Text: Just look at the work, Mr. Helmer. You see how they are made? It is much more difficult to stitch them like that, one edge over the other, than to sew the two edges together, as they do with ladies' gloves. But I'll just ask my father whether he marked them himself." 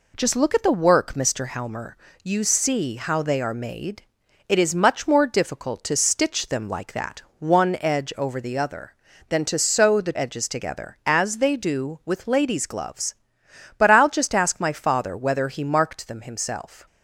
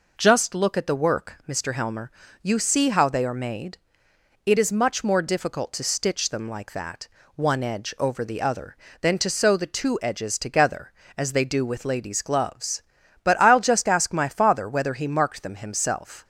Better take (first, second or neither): second